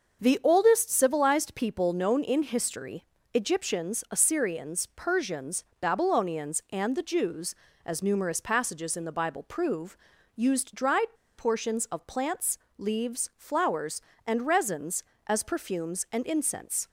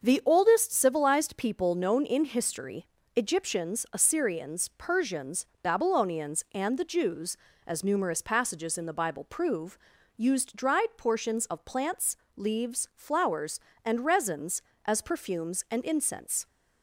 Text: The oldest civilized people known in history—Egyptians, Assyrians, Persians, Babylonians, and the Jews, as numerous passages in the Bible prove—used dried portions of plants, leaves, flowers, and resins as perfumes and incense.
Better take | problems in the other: second | starts louder than the rest; until 1.2 s; 6.5 dB; also in the second // pauses between "dried" and "portions"; slight; at 11.1 s; 0.22 s long

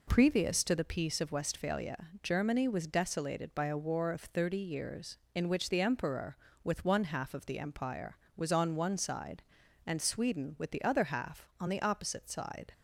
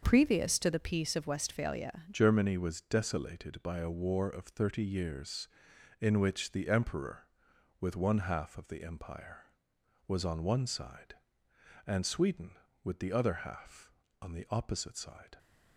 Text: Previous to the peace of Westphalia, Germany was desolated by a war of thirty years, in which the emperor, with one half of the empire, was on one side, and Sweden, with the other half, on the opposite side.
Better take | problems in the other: first | starts louder than the rest; until 1.0 s; 6.5 dB // changes voice at "Germany"; from 2.1 s on; 13.2 s long

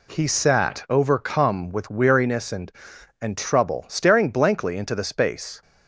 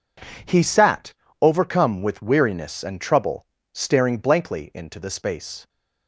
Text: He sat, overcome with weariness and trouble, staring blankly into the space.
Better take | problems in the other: second | says "and" twice; at 3.2 s

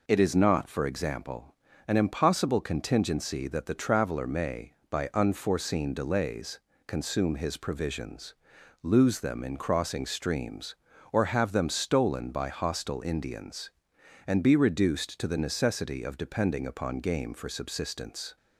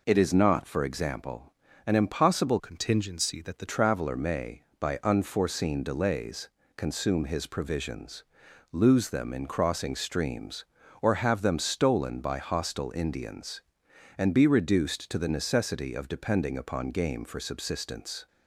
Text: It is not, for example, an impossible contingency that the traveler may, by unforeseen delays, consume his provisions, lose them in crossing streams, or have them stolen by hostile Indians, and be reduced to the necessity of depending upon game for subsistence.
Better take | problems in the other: first | changes voice from "contingency" to "the"; from 2.5 to 3.6 s; 1.1 s long

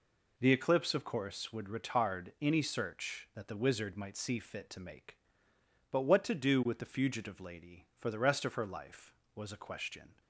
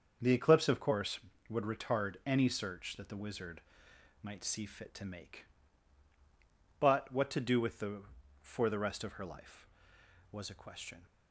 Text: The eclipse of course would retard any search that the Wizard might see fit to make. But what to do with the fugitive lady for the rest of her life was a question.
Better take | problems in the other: first | starts louder than the rest; until 1.5 s; 6.5 dB // pauses between "Wizard" and "might"; noticeable; at 3.6 s; 0.62 s long // skips "fugitive lady"; at 8.2 s

